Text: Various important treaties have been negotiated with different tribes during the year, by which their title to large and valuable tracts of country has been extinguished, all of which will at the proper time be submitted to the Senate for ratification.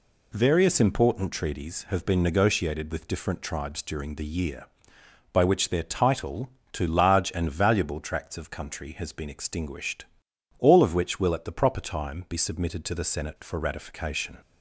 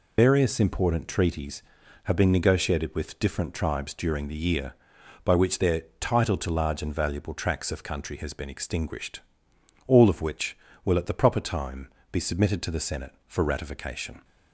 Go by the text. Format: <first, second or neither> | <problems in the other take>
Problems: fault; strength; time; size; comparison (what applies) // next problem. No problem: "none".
first | loses the start of "Various"; at 0.1 s; 110 ms // pauses between "their" and "title"; slight; at 5.8 s; 0.16 s long // pauses between "time" and "be"; slight; at 11.8 s; 0.24 s long